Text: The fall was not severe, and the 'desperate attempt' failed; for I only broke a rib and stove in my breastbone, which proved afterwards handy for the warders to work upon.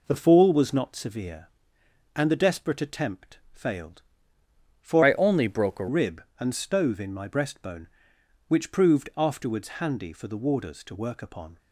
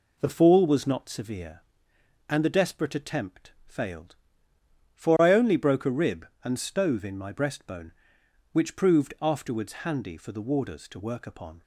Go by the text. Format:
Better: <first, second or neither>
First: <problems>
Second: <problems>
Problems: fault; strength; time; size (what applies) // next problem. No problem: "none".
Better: second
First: pauses between "attempt" and "failed"; slight; at 3.3 s; 0.16 s long // changes voice from "I" to "a"; from 5.0 to 5.8 s; 0.8 s long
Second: pauses between "attempt" and "failed"; slight; at 3.5 s; 0.16 s long